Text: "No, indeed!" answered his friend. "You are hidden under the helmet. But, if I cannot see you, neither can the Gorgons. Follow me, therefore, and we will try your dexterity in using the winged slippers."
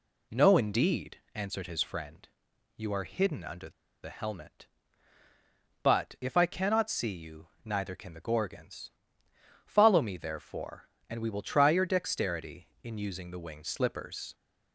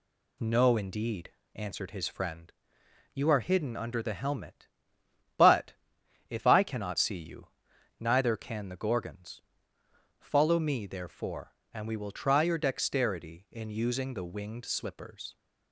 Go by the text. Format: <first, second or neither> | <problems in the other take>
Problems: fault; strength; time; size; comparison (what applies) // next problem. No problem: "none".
second | pauses between "under" and "the"; slight; at 3.6 s; 0.33 s long